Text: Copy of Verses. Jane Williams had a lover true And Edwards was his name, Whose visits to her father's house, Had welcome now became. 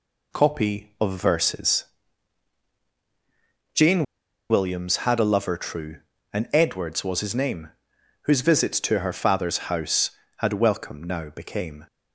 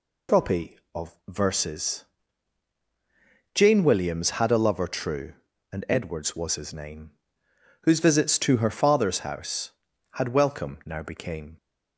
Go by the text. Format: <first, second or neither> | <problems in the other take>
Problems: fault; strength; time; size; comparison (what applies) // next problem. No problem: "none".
second | pauses between "Jane" and "Williams"; at 4.0 s; 0.45 s long